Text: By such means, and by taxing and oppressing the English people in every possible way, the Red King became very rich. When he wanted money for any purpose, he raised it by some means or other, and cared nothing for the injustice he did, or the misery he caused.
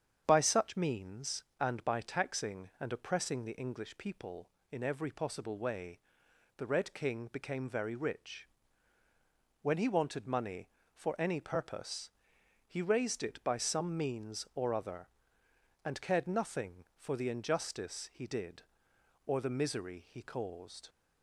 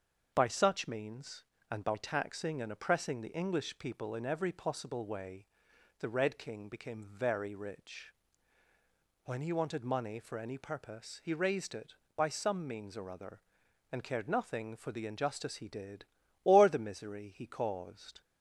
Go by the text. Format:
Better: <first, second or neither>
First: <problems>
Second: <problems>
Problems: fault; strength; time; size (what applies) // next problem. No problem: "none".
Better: neither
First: starts louder than the rest; strong; until 1.2 s; 8 dB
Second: starts louder than the rest; until 1.3 s; 6.5 dB